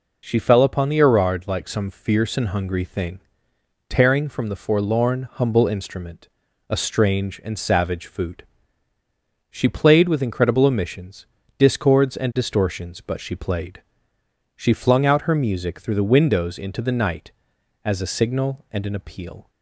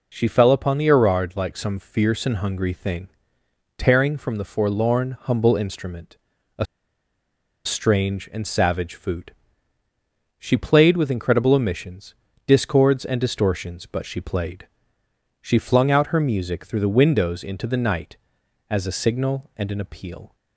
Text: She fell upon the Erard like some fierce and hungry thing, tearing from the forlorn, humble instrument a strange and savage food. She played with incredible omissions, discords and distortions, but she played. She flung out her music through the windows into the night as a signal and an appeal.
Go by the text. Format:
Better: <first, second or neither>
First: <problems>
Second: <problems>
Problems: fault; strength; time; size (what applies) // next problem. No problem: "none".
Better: first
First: pauses between "instrument" and "a"; at 6.2 s; 0.42 s long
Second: pauses between "instrument" and "a"; at 6.1 s; 0.42 s long // pauses between "a" and "strange"; at 6.6 s; 1.0 s long